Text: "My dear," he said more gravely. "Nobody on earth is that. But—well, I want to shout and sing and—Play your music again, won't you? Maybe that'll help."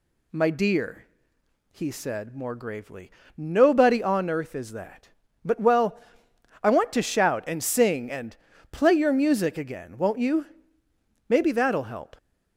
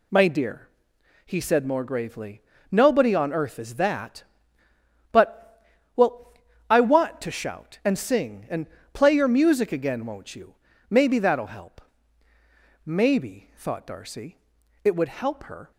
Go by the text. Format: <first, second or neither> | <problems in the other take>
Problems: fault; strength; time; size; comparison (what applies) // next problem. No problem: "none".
first | goes on to say "Maybe thought Darcy it would help her"; strong; from 12.8 s on; 2.8 s long